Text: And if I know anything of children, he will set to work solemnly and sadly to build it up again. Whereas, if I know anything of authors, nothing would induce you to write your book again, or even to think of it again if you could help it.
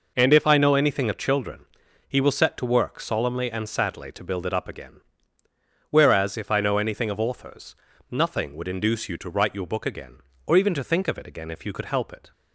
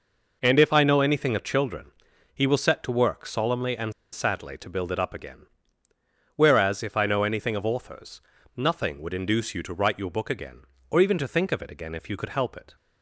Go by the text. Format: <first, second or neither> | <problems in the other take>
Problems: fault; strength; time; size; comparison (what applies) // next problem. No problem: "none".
first | pauses between "and" and "sadly"; slight; at 3.9 s; 0.20 s long